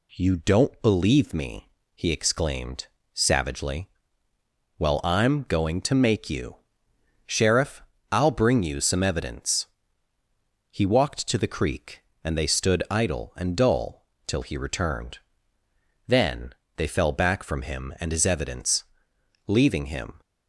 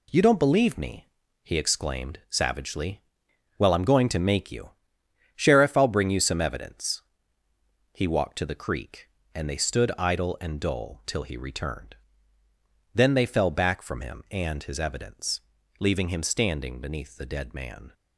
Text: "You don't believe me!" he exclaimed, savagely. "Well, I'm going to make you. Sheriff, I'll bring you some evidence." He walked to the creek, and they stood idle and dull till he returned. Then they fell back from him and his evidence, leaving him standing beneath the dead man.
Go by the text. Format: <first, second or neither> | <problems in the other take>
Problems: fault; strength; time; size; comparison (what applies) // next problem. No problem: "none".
second | pauses between "dull" and "till"; slight; at 14.0 s; 0.20 s long // pauses between "Then" and "they"; slight; at 16.5 s; 0.24 s long // stops before "standing beneath the dead man"; at 20.2 s